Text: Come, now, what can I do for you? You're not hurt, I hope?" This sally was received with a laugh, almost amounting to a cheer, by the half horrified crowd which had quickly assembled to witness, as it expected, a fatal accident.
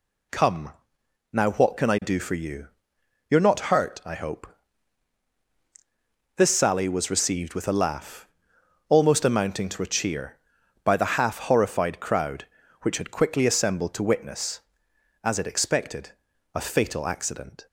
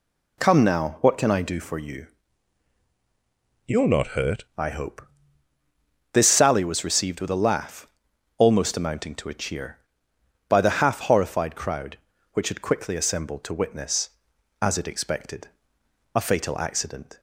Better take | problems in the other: first | changes voice from "You're" to "hurt"; from 3.6 to 4.4 s; 0.8 s long

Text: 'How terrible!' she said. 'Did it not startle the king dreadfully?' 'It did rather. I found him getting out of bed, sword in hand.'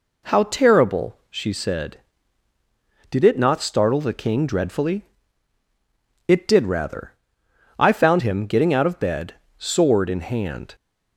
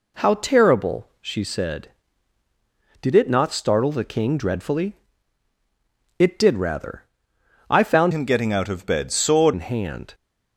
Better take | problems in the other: first | changes voice from "him" to "sword"; from 8.1 to 9.5 s; 1.4 s long

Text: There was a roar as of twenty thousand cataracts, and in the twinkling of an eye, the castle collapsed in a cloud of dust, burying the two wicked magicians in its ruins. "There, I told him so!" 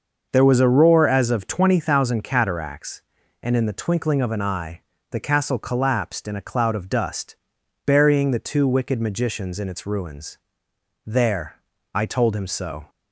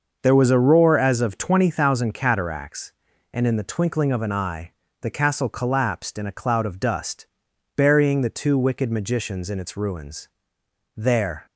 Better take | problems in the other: first | starts louder than the rest; until 1.2 s; 6 dB; also in the first // stops before "I told him so"; at 11.4 s

